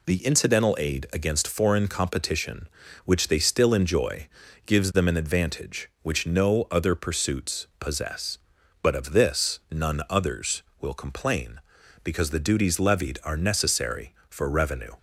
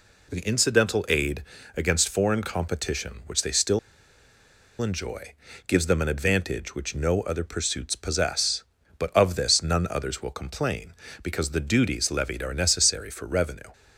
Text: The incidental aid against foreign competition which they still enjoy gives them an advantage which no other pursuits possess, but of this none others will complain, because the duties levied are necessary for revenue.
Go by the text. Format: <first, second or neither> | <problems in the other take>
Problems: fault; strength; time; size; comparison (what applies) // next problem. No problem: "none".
first | pauses between "aid" and "against"; slight; at 1.4 s; 0.32 s long // pauses between "still" and "enjoy"; at 3.7 s; 1.0 s long // pauses between "enjoy" and "gives"; slight; at 5.3 s; 0.34 s long; also in the first